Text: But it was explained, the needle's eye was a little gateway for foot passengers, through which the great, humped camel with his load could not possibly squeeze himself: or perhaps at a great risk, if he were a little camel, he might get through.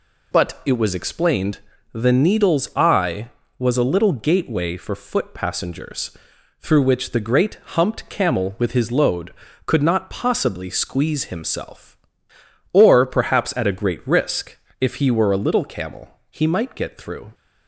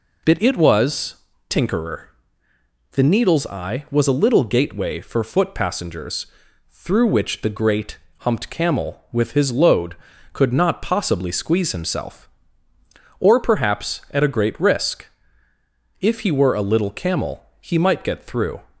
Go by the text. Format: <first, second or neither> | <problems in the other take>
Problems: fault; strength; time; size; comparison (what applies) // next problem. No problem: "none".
first | says "tinkerer" for "explained"; at 1.5 s